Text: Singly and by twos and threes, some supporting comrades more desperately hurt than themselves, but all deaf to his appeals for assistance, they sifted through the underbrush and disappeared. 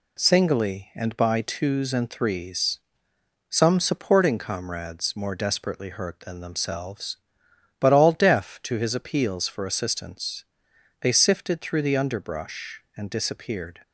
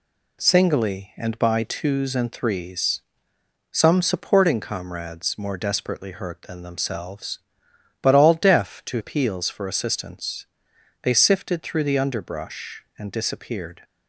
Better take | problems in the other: first | skips "his"; at 8.9 s

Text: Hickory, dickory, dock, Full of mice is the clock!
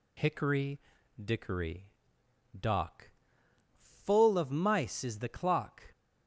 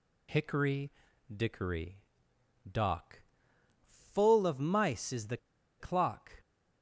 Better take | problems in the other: first | pauses between "the" and "clock"; at 5.3 s; 0.42 s long

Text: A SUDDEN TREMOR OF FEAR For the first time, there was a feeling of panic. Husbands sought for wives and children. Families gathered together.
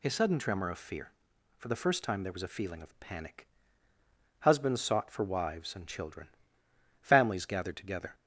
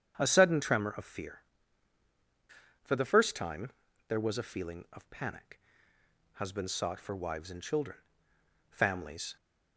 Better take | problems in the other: first | starts louder than the rest; strong; until 1.1 s; 8.5 dB // stops before "gathered together"; at 9.3 s

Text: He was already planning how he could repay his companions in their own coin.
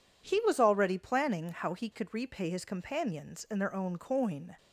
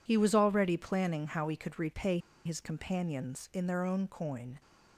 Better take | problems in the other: first | pauses between "repay" and "his"; slight; at 2.1 s; 0.25 s long

